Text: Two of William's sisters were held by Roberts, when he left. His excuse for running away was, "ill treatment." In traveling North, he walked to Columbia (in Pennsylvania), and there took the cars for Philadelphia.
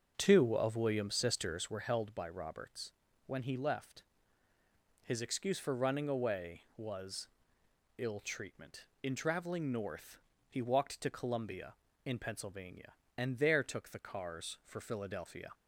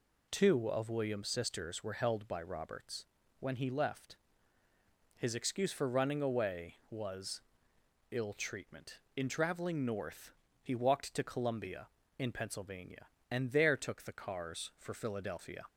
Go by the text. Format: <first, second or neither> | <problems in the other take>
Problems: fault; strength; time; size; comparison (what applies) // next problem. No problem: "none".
second | starts louder than the rest; noticeable; until 1.8 s; 6 dB